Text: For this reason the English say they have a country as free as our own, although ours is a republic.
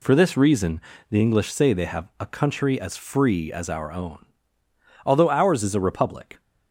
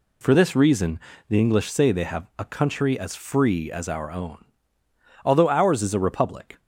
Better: neither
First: pauses between "reason" and "the"; slight; at 0.8 s; 0.30 s long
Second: pauses between "reason" and "the"; slight; at 0.9 s; 0.30 s long

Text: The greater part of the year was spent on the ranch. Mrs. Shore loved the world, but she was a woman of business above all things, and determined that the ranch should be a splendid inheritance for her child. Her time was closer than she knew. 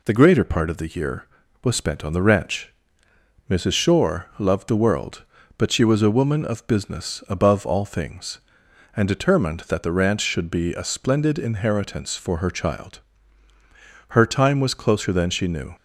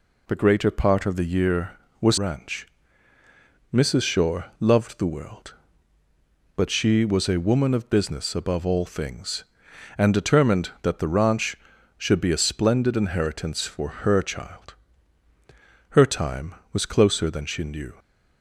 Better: first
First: none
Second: skips "spent on the"; at 2.1 s

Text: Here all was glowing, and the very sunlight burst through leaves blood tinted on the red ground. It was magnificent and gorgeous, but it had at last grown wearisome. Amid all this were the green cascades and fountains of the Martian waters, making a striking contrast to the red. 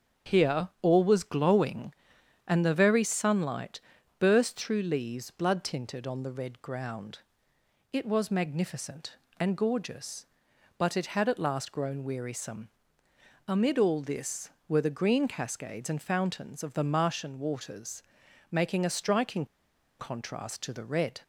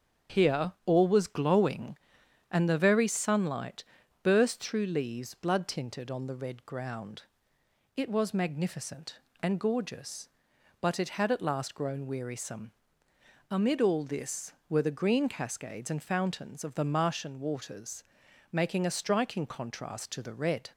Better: second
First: starts louder than the rest; strong; until 1.4 s; 7.5 dB // pauses between "sunlight" and "burst"; at 3.7 s; 0.40 s long // pauses between "striking" and "contrast"; noticeable; at 19.4 s; 0.54 s long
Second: starts louder than the rest; strong; until 1.4 s; 7.5 dB // pauses between "sunlight" and "burst"; at 3.8 s; 0.40 s long

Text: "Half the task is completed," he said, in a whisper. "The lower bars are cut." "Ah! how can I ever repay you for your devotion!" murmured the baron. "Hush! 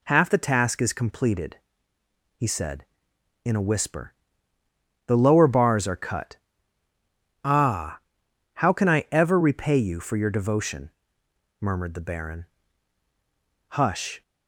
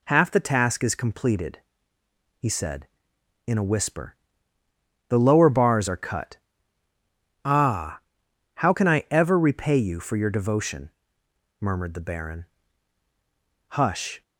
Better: neither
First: none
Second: none

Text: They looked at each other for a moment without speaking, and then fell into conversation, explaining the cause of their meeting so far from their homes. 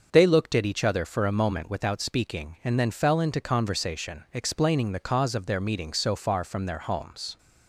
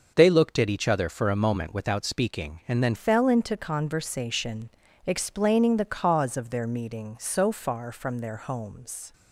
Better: first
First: starts louder than the rest; until 1.1 s; 6.5 dB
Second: starts louder than the rest; until 1.1 s; 6.5 dB // changes voice at "fell"; from 2.9 s on; 6.2 s long

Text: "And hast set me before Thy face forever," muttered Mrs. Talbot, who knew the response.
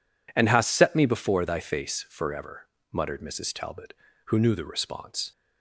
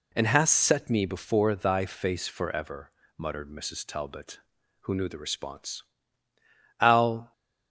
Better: first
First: none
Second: goes on to say "Al"; from 6.8 s on; 0.50 s long

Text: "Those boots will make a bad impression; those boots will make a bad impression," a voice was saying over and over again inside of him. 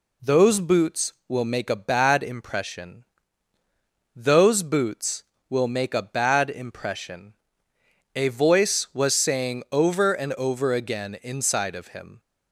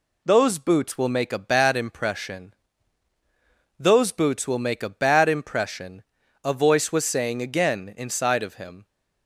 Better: first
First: none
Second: skips "over and over"; at 7.4 s

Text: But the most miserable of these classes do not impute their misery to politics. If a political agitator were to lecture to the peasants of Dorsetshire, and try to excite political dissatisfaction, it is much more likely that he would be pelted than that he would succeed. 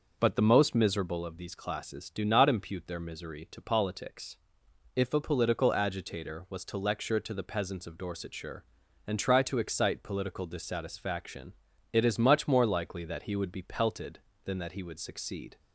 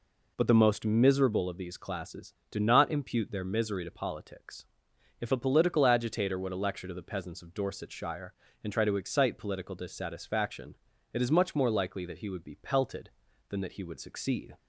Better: second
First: says "was" for "were"; at 6.4 s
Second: none

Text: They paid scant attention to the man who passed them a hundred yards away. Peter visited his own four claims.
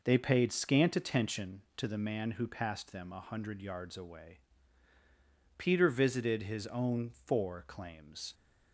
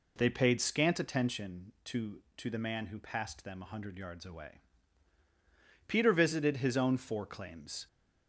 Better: first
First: none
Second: says "to" twice; at 2.3 s

